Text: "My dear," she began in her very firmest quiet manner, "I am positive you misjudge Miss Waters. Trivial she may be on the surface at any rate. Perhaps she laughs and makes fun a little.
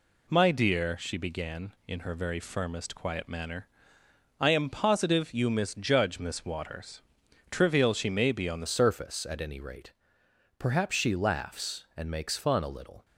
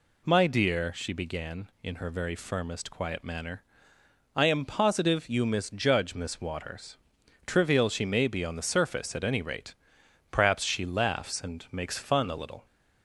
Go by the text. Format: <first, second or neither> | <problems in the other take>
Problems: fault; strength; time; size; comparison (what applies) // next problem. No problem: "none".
second | changes voice at "surface"; from 8.6 s on; 4.4 s long